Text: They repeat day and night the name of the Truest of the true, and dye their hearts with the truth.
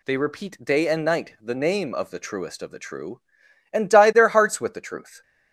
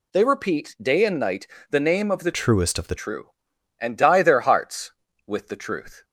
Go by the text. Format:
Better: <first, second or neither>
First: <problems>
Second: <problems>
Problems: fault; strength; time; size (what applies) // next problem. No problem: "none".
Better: first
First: none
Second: pauses between "night" and "the"; slight; at 1.4 s; 0.24 s long // changes voice from "Truest" to "the"; from 2.3 to 2.9 s; 0.6 s long